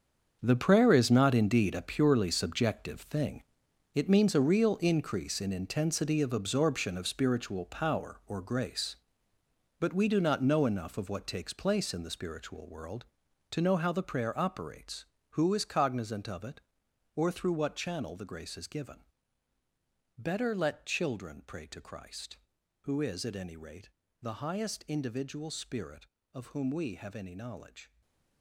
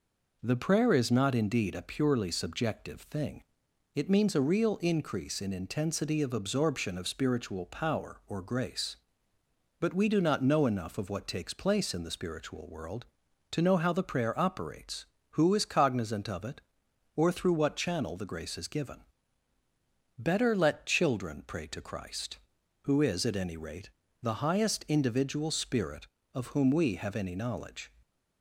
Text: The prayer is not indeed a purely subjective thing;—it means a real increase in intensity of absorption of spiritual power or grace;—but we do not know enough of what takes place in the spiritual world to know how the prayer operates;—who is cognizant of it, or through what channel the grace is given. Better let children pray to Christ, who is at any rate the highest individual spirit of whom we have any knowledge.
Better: second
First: gets quieter; strong; throughout; 12 dB // pauses between "rate" and "the"; slight; at 23.8 s; 0.32 s long // stays silent after the last word; slight; from 27.8 s on; 0.6 s long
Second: pauses between "rate" and "the"; slight; at 23.8 s; 0.32 s long

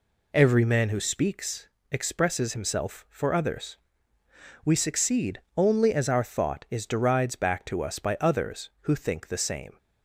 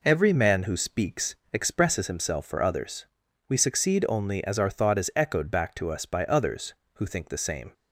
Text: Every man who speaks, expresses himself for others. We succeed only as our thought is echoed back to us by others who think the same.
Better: second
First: pauses between "succeed" and "only"; slight; at 5.3 s; 0.16 s long // says "derides" for "echoed"; at 6.8 s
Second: none

